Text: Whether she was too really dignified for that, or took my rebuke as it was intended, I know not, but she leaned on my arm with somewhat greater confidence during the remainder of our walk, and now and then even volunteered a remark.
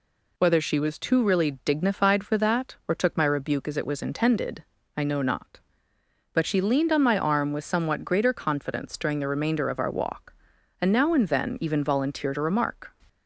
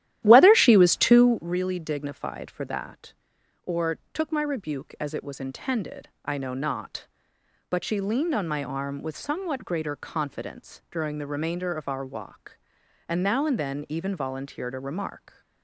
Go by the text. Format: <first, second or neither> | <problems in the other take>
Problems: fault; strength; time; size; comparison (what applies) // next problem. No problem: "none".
first | starts louder than the rest; strong; until 1.5 s; 13 dB